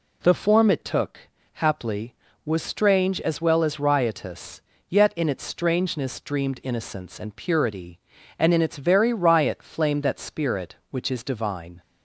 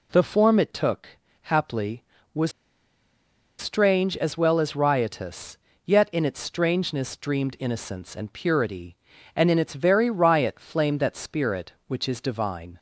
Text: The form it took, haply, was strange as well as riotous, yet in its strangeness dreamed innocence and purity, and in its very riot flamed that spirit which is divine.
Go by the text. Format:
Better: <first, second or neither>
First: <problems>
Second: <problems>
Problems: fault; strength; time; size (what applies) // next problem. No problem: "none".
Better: first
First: none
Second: pauses between "was" and "strange"; at 2.5 s; 1.0 s long